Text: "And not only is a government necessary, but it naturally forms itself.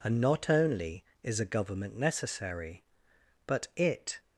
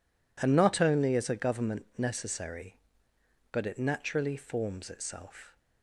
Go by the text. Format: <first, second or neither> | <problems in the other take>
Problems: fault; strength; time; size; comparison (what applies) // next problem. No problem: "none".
second | stops before "naturally forms itself"; at 4.1 s